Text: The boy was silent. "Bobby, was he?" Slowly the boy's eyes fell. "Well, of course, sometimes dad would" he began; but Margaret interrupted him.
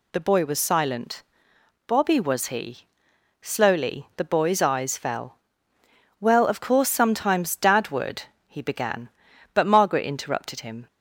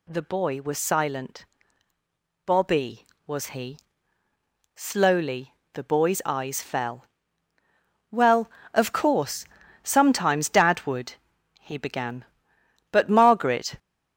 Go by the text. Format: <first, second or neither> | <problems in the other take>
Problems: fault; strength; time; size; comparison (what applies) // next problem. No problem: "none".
first | pauses between "Slowly" and "the"; slight; at 5.5 s; 0.22 s long // pauses between "would" and "he"; at 11.1 s; 0.44 s long; slight in the first // stops before "interrupted him"; at 13.7 s